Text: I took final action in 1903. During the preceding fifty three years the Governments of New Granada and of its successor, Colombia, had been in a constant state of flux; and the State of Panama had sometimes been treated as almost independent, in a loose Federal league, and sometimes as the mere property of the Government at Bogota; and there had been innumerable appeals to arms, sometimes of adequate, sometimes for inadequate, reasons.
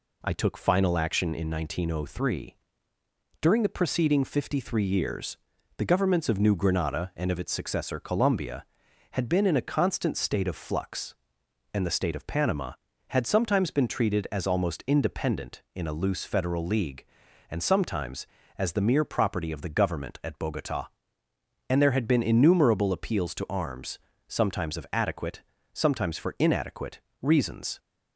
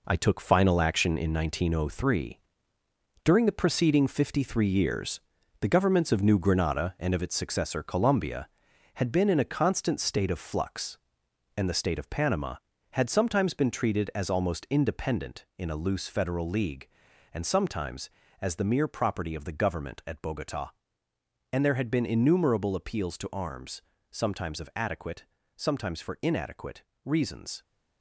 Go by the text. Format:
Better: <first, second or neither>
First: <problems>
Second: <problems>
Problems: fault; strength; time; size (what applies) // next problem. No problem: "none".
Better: first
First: pauses between "years" and "the"; at 5.3 s; 0.40 s long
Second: gets quieter; strong; throughout; 7.5 dB // pauses between "years" and "the"; at 5.1 s; 0.40 s long